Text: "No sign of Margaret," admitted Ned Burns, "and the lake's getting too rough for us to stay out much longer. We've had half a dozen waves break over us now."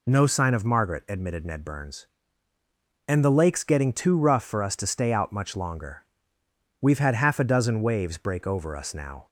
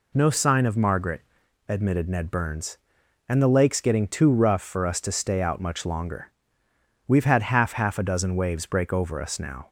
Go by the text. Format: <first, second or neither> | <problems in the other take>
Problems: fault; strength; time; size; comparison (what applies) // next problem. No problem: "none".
first | says "half" twice; at 7.7 s